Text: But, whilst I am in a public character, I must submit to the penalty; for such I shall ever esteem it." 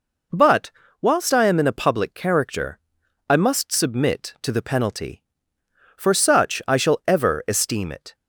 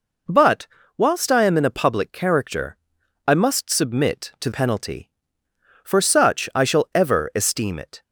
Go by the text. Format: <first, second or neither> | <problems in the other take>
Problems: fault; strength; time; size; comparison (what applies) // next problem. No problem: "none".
first | skips "the"; at 4.5 s